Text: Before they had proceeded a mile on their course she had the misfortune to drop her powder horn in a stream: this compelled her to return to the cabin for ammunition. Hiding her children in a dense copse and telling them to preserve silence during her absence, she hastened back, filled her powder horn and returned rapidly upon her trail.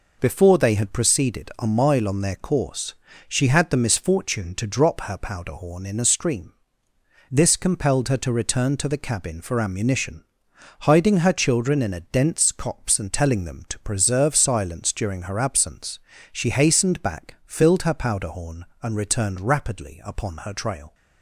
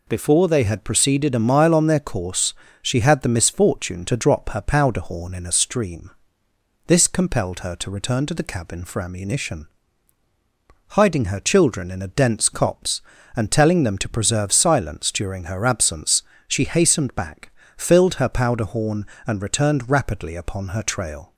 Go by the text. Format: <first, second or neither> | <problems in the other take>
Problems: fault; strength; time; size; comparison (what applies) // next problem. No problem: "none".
neither | pauses between "course" and "she"; slight; the same in both